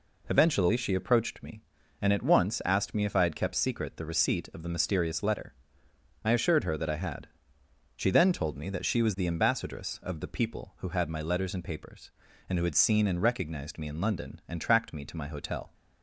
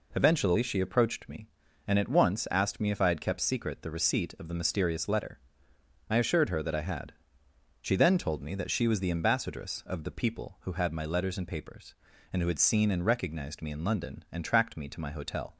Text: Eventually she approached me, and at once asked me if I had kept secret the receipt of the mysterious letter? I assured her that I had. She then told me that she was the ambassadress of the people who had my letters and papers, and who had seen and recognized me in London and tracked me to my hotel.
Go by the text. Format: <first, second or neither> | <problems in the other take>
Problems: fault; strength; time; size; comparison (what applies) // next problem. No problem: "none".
neither | none